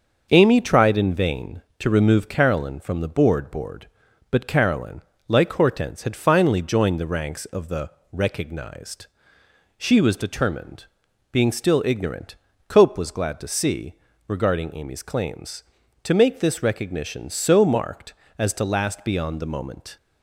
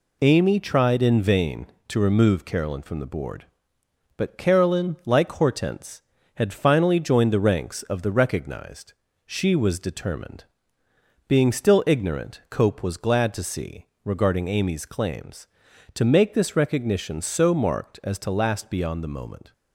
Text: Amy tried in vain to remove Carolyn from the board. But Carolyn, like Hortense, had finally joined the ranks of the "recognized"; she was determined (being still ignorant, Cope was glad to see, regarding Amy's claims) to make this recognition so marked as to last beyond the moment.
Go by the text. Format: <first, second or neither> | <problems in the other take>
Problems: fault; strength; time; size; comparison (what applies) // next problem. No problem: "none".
second | starts louder than the rest; until 1.3 s; 6 dB // says "board" twice; at 3.5 s // pauses between "the" and "recognized"; slight; at 7.8 s; 0.24 s long